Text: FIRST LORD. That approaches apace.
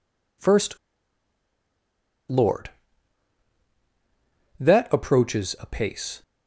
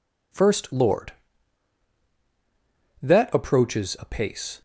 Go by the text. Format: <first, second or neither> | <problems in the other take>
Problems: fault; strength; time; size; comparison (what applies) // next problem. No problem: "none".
second | pauses between "FIRST" and "LORD"; strong; at 0.7 s; 1.5 s long